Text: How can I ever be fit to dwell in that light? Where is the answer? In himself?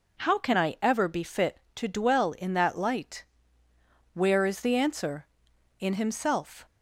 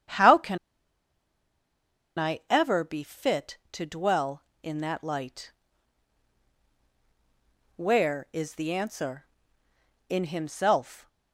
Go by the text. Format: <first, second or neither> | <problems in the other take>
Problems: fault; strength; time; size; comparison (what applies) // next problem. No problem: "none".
first | starts louder than the rest; strong; until 2.8 s; 8.5 dB // pauses between "can" and "I"; strong; at 0.5 s; 1.5 s long